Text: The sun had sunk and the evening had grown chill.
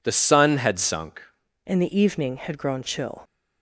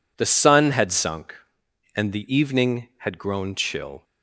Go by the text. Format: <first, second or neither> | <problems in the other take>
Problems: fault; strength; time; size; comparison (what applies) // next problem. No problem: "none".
second | changes voice at "and"; from 1.6 s on; 1.6 s long